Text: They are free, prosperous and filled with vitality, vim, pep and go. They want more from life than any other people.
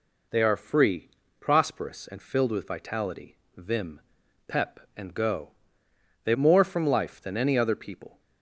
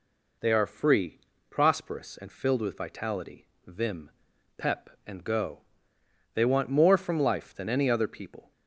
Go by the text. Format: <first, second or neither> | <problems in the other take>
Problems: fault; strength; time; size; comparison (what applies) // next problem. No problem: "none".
second | skips "want"; at 6.3 s